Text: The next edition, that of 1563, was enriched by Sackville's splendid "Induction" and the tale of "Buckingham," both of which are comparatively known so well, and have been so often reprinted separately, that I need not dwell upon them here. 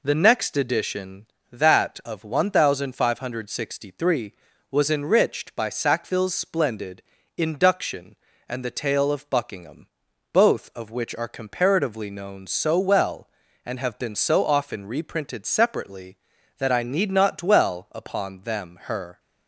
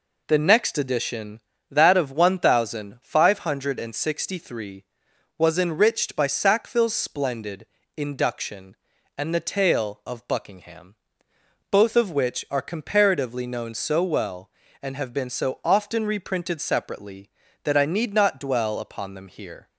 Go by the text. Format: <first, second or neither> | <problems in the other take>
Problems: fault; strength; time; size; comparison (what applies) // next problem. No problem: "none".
second | pauses between "splendid" and "Induction"; slight; at 7.0 s; 0.34 s long; slight in the second // says "her" for "here"; at 18.8 s